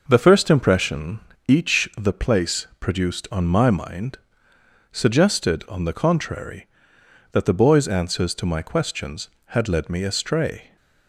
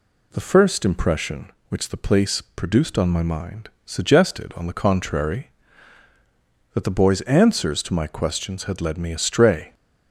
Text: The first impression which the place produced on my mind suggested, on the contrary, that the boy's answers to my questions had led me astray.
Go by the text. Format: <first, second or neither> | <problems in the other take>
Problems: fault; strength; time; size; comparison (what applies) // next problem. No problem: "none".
second | says "each" for "which"; at 1.4 s // pauses between "mind" and "suggested"; noticeable; at 4.1 s; 0.74 s long; slight in the second